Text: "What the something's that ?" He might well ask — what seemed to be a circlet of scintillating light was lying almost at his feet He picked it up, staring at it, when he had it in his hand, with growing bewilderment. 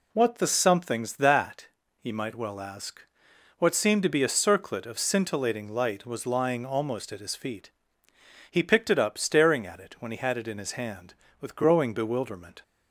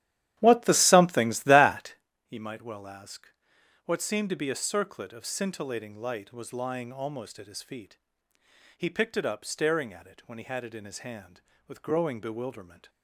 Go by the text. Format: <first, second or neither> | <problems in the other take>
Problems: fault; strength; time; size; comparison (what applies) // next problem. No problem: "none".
first | starts louder than the rest; strong; until 2.1 s; 12 dB // pauses between "feet" and "He"; noticeable; at 7.9 s; 0.80 s long; noticeable in the first